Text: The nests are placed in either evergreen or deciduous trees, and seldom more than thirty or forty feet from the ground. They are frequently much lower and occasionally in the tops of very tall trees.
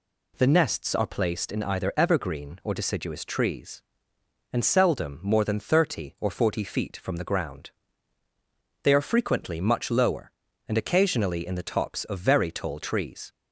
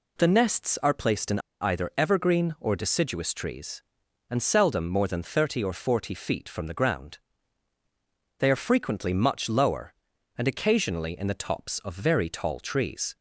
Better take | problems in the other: first | pauses between "in" and "either"; slight; at 1.3 s; 0.22 s long

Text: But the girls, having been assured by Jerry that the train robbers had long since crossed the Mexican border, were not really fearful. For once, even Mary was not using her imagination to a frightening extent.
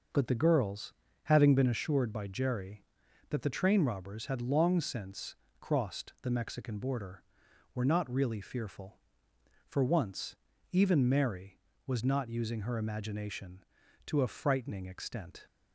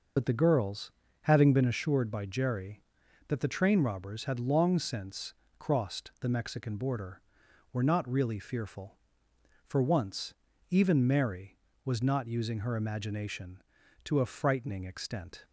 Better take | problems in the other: first | loses the start of "But"; at 0.1 s; 65 ms // pauses between "since" and "crossed"; slight; at 5.3 s; 0.24 s long; slight in the first

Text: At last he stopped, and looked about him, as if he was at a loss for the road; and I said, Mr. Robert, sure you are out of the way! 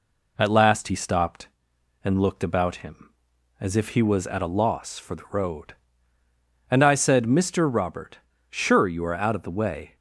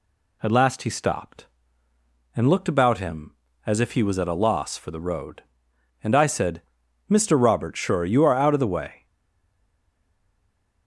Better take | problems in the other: first | stays silent after the last word; noticeable; from 9.0 s on; 1.8 s long

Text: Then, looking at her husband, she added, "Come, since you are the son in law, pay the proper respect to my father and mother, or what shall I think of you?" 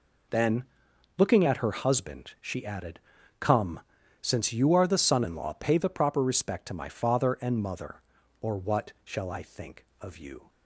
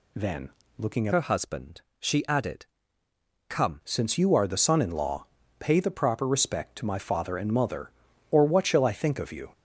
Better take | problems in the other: first | changes voice from "her" to "Come"; from 1.1 to 3.8 s; 2.7 s long

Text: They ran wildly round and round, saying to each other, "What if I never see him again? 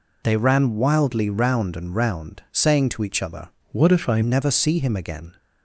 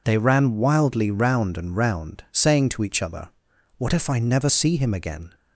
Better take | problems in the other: second | changes voice from "What" to "I"; from 3.7 to 4.2 s; 0.5 s long

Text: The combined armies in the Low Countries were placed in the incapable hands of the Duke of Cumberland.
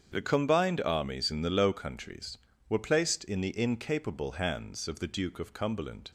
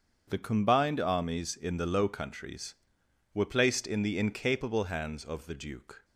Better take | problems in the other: first | starts louder than the rest; strong; until 1.3 s; 7 dB; strong in the first // stops before "of Cumberland"; at 6.0 s

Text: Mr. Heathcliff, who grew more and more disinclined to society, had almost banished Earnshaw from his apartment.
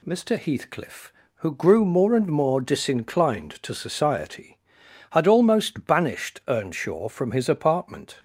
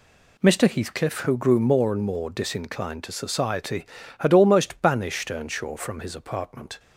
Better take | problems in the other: neither | none

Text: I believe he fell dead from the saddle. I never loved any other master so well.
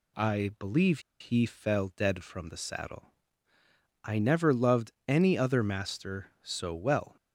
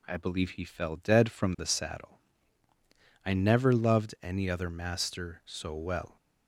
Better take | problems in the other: second | pauses between "believe" and "he"; slight; at 0.9 s; 0.20 s long // pauses between "loved" and "any"; slight; at 4.9 s; 0.16 s long

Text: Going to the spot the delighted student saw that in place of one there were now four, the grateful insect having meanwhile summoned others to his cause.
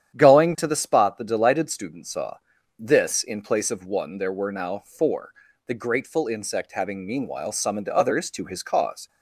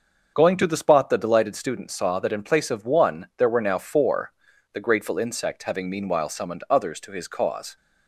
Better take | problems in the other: second | starts louder than the rest; strong; until 1.1 s; 9.5 dB; also in the second // says "this" for "that"; at 2.7 s

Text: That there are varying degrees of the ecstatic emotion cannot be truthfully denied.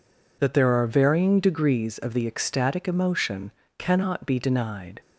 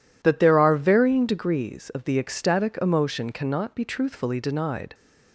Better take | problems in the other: second | pauses between "emotion" and "cannot"; slight; at 3.5 s; 0.26 s long // skips "truthfully"; at 4.3 s

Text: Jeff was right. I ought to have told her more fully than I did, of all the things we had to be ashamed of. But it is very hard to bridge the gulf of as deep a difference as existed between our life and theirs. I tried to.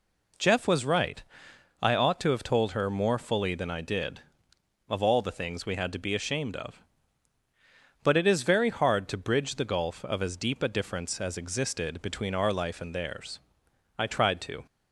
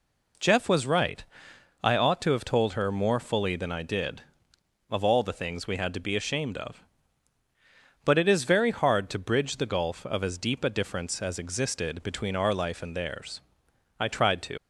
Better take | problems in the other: first | leaves "to" unfinished; at 14.5 s; 90 ms

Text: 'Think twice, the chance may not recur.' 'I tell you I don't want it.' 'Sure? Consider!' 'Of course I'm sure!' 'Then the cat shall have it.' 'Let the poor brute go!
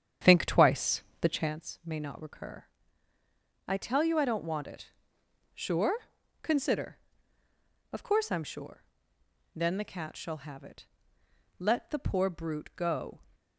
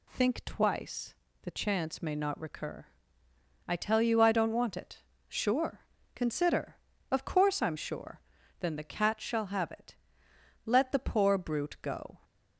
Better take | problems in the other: second | starts louder than the rest; strong; until 1.6 s; 8.5 dB

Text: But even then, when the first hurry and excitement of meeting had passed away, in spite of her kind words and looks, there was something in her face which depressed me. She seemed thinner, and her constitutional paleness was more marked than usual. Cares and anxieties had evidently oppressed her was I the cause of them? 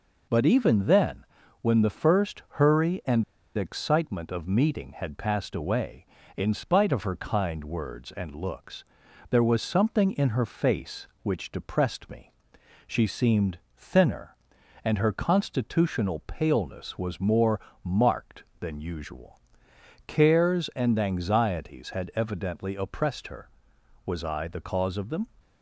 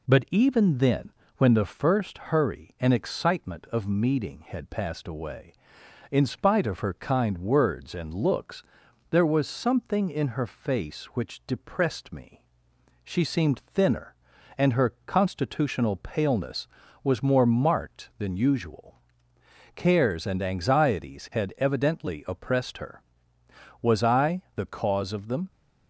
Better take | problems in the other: second | pauses between "and" and "excitement"; slight; at 3.2 s; 0.33 s long // pauses between "seemed" and "thinner"; slight; at 13.5 s; 0.20 s long // pauses between "more" and "marked"; slight; at 17.5 s; 0.24 s long

